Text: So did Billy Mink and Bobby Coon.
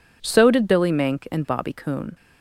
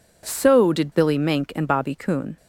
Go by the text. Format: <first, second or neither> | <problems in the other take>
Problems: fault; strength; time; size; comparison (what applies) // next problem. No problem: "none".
neither | none